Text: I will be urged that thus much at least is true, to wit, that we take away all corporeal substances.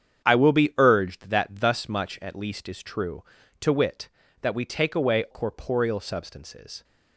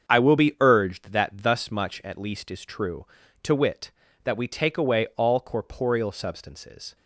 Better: second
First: starts louder than the rest; strong; until 1.2 s; 8 dB // skips "all"; at 5.2 s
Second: starts louder than the rest; until 1.1 s; 7 dB

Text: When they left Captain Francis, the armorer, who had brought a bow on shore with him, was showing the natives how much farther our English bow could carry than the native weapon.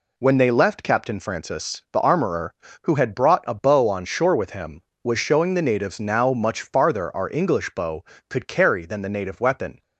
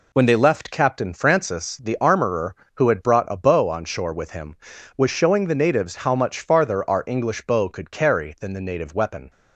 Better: second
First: says "now" for "how"; at 5.9 s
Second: none

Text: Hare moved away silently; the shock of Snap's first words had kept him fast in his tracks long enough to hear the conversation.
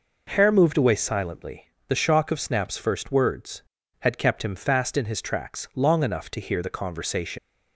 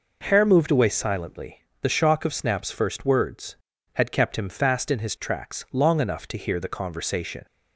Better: second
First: leaves "conversation" unfinished; at 7.3 s; 85 ms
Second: none

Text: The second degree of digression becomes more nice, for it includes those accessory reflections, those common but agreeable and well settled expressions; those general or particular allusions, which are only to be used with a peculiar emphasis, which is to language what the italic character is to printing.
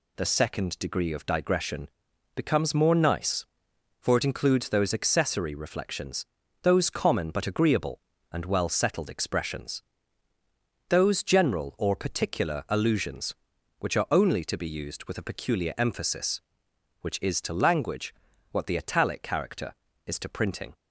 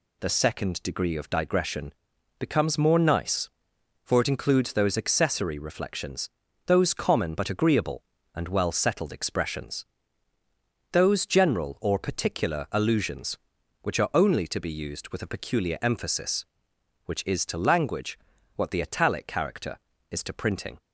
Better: neither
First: pauses between "digression" and "becomes"; noticeable; at 1.8 s; 0.46 s long // pauses between "language" and "what"; at 18.1 s; 0.38 s long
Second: pauses between "digression" and "becomes"; noticeable; at 1.9 s; 0.46 s long // pauses between "language" and "what"; at 18.1 s; 0.38 s long

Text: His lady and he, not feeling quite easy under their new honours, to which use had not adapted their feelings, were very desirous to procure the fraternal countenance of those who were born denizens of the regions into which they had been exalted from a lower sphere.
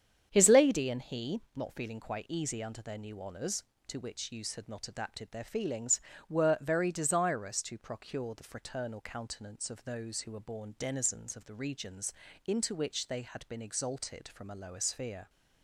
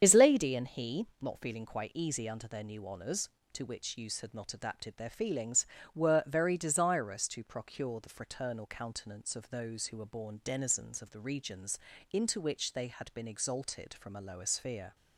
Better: first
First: starts louder than the rest; strong; until 1.3 s; 8 dB // pauses between "regions" and "into"; slight; at 12.1 s; 0.32 s long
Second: loses the start of "His"; at 0.0 s; 55 ms // starts louder than the rest; strong; until 1.0 s; 8 dB // pauses between "regions" and "into"; slight; at 11.7 s; 0.32 s long

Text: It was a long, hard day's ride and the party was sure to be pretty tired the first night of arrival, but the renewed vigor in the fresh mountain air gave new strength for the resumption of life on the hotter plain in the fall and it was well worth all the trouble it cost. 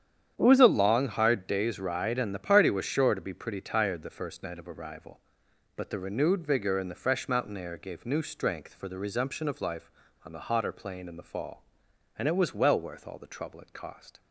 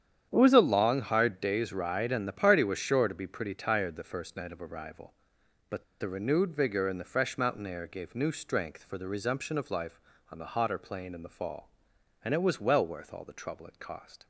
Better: first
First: starts louder than the rest; strong; until 1.3 s; 9 dB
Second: starts louder than the rest; strong; until 1.3 s; 9 dB // pauses between "but" and "the"; slight; at 5.8 s; 0.16 s long

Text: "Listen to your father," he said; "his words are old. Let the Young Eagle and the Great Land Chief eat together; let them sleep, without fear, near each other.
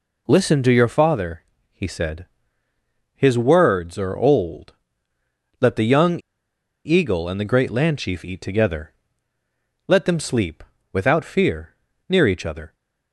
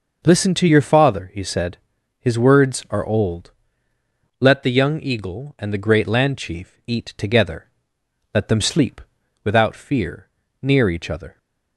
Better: second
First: pauses between "Young" and "Eagle"; noticeable; at 6.1 s; 0.65 s long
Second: none

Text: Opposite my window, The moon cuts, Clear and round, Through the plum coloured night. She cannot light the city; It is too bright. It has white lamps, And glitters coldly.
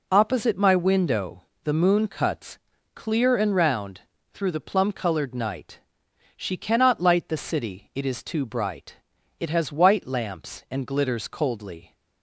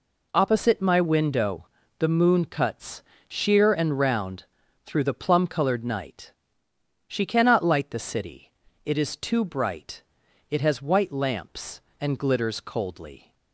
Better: first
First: none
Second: says "Sheer" for "Clear"; at 3.2 s

